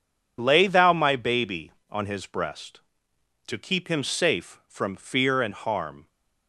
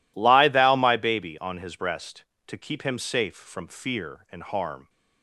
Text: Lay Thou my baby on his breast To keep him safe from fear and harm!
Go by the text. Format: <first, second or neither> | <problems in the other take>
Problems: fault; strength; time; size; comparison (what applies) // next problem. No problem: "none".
first | says "Lie" for "Lay"; at 0.1 s